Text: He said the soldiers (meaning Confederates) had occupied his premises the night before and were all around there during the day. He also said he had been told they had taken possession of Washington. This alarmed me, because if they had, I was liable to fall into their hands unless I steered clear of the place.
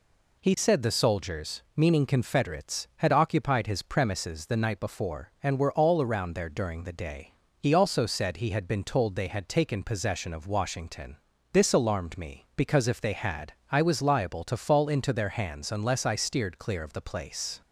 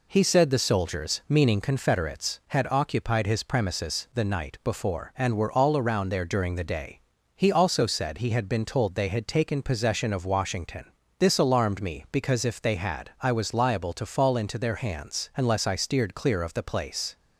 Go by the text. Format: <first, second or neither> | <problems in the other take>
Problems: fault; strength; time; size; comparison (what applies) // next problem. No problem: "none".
neither | none